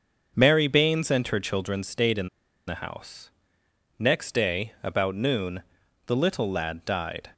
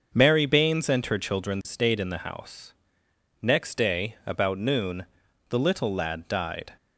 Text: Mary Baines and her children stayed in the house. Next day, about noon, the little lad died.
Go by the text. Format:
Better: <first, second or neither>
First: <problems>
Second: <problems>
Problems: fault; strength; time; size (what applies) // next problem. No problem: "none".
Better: second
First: starts louder than the rest; until 1.4 s; 7 dB // pauses between "in" and "the"; at 2.2 s; 0.40 s long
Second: starts louder than the rest; until 1.1 s; 7 dB